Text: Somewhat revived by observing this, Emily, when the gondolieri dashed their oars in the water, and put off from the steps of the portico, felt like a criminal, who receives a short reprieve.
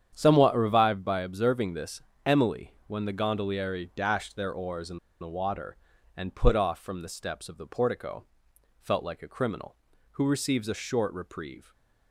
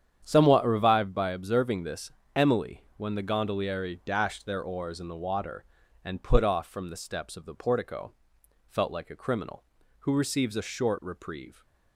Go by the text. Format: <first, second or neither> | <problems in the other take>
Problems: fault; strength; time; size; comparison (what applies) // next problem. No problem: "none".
second | starts louder than the rest; strong; until 1.1 s; 9 dB; strong in the second // pauses between "in" and "the"; slight; at 4.9 s; 0.22 s long // stays silent after the last word; slight; from 11.6 s on; 0.5 s long